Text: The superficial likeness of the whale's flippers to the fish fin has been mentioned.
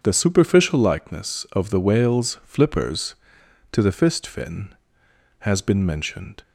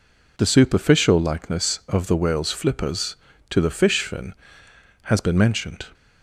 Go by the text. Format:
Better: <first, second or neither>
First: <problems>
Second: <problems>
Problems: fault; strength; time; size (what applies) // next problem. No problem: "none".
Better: second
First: starts louder than the rest; until 1.0 s; 7 dB // says "fist" for "fish"; at 3.9 s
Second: none